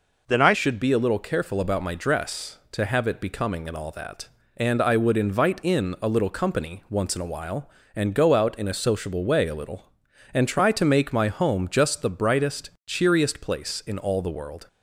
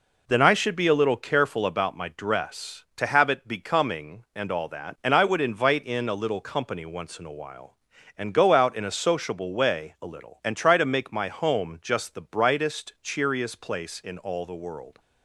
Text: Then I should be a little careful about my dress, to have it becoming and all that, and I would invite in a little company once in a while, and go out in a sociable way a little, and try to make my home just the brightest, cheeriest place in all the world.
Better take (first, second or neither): second